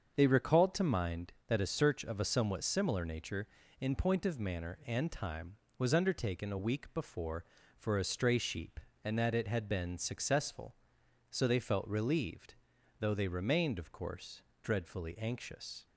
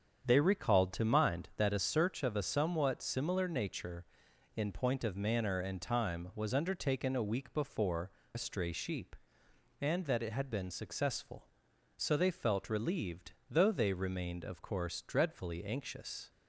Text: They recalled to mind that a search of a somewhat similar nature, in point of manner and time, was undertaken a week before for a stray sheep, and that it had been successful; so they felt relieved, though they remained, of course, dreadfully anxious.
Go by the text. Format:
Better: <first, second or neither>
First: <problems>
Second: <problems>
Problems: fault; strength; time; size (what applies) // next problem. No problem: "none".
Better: first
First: starts louder than the rest; until 1.1 s; 6.5 dB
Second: starts louder than the rest; strong; until 1.3 s; 8 dB // skips "for"; at 8.2 s